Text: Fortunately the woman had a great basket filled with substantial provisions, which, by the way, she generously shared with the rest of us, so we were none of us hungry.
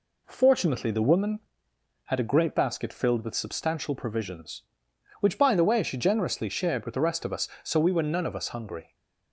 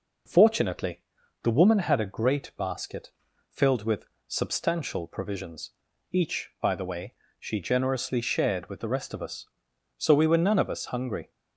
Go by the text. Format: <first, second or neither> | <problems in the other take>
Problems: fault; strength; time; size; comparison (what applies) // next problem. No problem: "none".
first | pauses between "Fortunately" and "the"; at 1.0 s; 0.40 s long // pauses between "basket" and "filled"; at 3.1 s; 0.38 s long // pauses between "with" and "substantial"; slight; at 4.0 s; 0.20 s long // says "each" for "which"; at 6.1 s